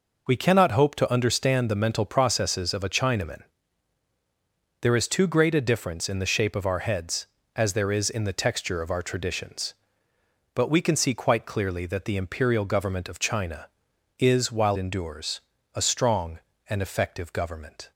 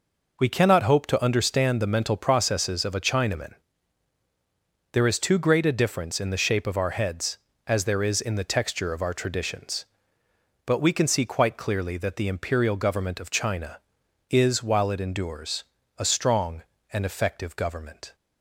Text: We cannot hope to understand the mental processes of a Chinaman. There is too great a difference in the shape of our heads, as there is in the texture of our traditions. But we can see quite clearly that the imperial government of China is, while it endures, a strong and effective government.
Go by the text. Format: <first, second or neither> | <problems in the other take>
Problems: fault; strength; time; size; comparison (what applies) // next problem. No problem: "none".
second | skips "it"; at 14.7 s